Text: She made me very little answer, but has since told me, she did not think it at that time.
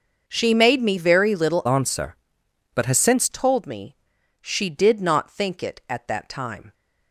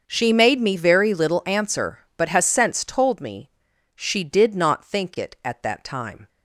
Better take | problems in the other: second | starts louder than the rest; noticeable; until 1.3 s; 6 dB; also in the second // changes voice from "answer" to "since"; from 1.6 to 3.2 s; 1.6 s long

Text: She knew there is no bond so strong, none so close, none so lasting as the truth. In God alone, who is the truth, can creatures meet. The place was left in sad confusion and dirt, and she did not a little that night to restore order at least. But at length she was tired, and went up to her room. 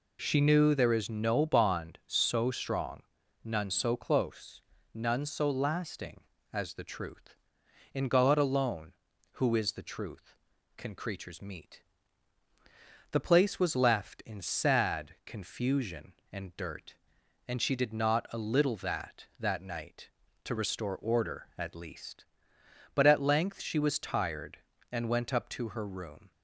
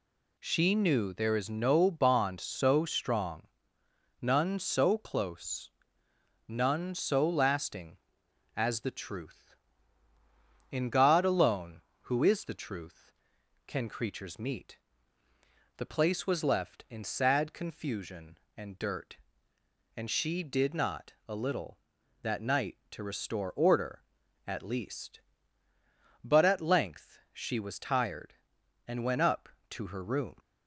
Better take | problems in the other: second | says "that" twice; at 19.3 s

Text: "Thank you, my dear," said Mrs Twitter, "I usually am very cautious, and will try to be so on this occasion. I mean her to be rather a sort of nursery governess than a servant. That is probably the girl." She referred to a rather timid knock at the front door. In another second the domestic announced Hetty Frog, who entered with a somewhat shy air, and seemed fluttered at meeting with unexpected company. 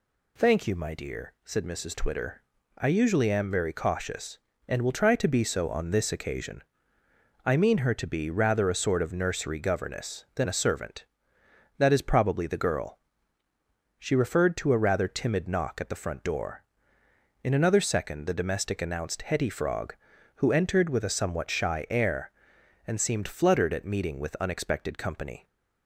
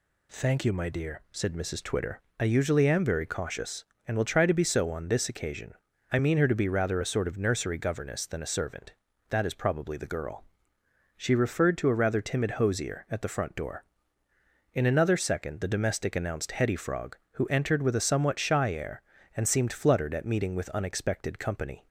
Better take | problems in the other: first | says "hosier" for "knock"; at 12.5 s

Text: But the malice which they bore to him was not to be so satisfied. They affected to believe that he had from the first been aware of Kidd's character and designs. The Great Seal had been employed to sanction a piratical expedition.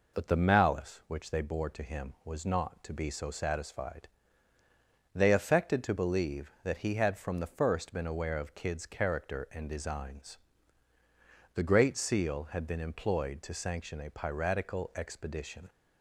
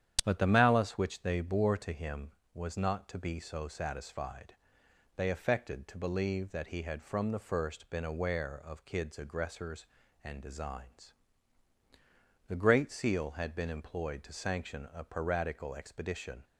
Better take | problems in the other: first | starts louder than the rest; strong; until 1.2 s; 9.5 dB // says "aggressors" for "character"; at 9.1 s

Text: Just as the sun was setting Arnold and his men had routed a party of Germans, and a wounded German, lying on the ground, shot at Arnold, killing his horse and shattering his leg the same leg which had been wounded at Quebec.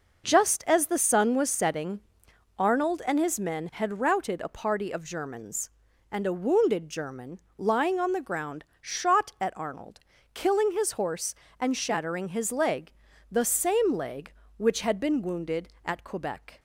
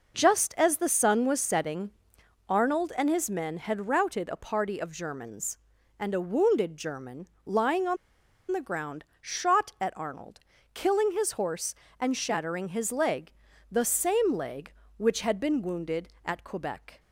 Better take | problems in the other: first | pauses between "setting" and "Arnold"; noticeable; at 1.8 s; 0.58 s long; noticeable in the first // pauses between "on" and "the"; noticeable; at 7.9 s; 0.55 s long // pauses between "leg" and "the"; at 13.3 s; 0.40 s long; also in the first

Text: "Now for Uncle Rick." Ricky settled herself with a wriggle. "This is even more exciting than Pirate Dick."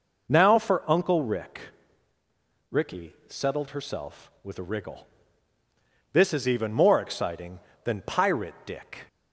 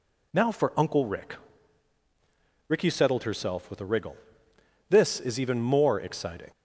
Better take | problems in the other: first | stops before "than Pirate Dick"; at 6.5 s

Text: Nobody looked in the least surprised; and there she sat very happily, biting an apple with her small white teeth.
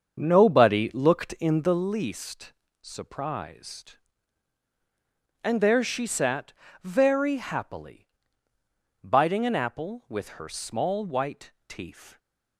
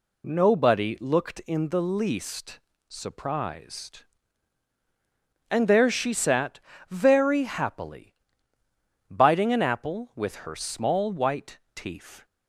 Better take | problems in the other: second | starts louder than the rest; until 1.9 s; 7 dB // pauses between "least" and "surprised"; slight; at 2.5 s; 0.30 s long; slight in the second // pauses between "sat" and "very"; slight; at 6.5 s; 0.30 s long; slight in the second // pauses between "white" and "teeth"; slight; at 11.5 s; 0.16 s long; slight in the second

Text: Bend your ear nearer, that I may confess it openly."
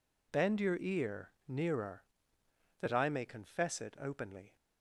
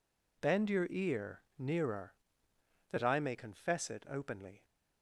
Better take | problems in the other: neither | pauses between "ear" and "nearer"; slight; the same in both

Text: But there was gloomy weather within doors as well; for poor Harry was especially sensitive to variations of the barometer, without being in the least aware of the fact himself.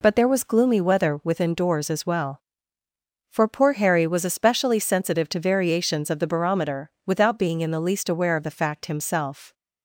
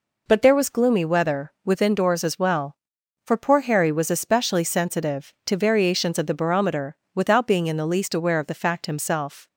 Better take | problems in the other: neither | none

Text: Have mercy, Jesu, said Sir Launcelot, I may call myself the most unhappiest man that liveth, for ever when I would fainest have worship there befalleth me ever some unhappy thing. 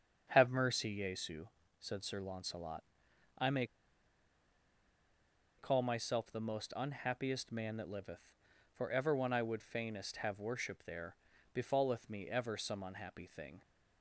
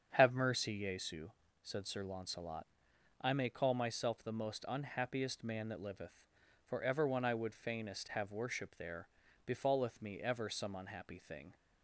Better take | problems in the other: second | starts louder than the rest; strong; until 1.3 s; 7.5 dB; strong in the second // pauses between "may" and "call"; strong; at 3.6 s; 1.9 s long // pauses between "there" and "befalleth"; at 11.1 s; 0.38 s long; also in the second

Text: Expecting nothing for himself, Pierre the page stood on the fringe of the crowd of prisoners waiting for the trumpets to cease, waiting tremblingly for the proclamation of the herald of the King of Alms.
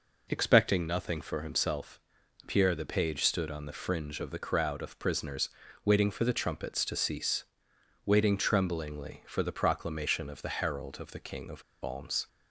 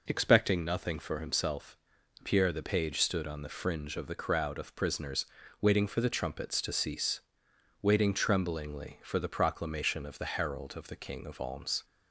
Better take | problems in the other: second | pauses between "prisoners" and "waiting"; at 5.4 s; 0.38 s long; also in the second // pauses between "of" and "Alms"; slight; at 11.6 s; 0.21 s long

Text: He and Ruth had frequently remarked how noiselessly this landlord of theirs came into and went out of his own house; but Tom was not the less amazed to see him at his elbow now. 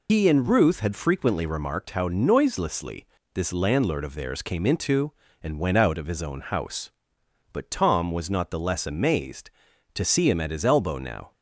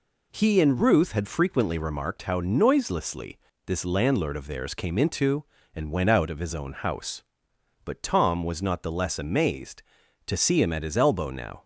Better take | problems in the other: second | loses the start of "He"; at 0.0 s; 110 ms // pauses between "noiselessly" and "this"; slight; at 3.0 s; 0.28 s long; slight in the second

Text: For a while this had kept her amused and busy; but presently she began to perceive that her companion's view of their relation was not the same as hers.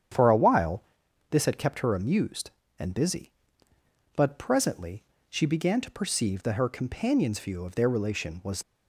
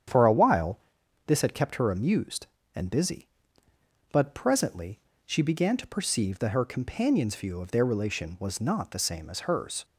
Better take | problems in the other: second | starts louder than the rest; strong; until 1.6 s; 9 dB; strong in the second // pauses between "while" and "this"; noticeable; at 0.8 s; 0.48 s long; noticeable in the second // pauses between "presently" and "she"; slight; at 5.0 s; 0.26 s long; slight in the second // stops before "not the same as hers"; at 8.6 s

